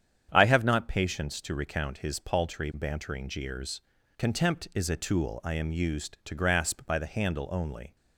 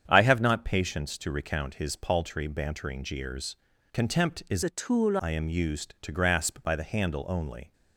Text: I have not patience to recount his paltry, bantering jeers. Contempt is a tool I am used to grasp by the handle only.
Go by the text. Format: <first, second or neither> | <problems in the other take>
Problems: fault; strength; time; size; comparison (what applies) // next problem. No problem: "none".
first | starts louder than the rest; strong; until 1.0 s; 8.5 dB; strong in the first // changes voice from "a" to "tool"; from 4.6 to 5.1 s; 0.5 s long